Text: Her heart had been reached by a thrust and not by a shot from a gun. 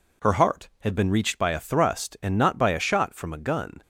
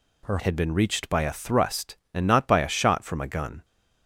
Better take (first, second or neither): first